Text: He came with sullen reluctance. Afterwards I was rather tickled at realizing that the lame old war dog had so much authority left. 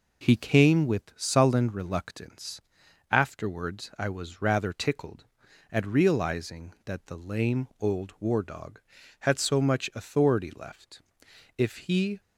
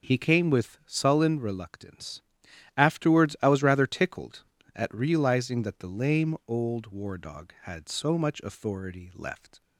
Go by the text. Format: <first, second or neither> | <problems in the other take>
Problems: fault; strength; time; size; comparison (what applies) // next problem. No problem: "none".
second | goes on to say "If he"; noticeable; from 11.5 s on; 0.62 s long